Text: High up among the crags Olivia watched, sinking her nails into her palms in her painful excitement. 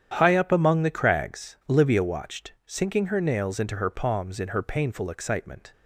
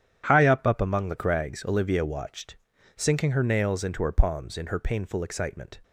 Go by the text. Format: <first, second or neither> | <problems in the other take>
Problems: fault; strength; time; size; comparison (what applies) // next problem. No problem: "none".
first | starts louder than the rest; strong; until 1.2 s; 10.5 dB; strong in the first // says "up" twice; at 0.6 s